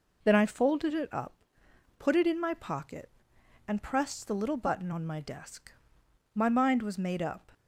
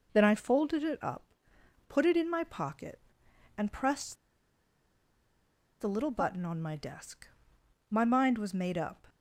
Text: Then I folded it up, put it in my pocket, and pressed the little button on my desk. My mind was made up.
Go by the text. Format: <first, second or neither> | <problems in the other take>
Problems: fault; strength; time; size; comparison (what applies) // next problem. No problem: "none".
first | pauses between "pressed" and "the"; strong; at 4.1 s; 1.6 s long